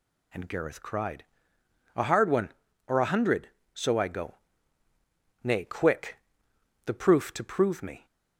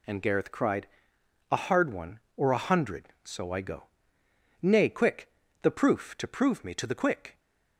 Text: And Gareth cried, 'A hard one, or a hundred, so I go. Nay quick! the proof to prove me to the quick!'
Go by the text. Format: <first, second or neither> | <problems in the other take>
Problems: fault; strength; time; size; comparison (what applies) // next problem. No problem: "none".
second | stops before "to the quick"; at 8.0 s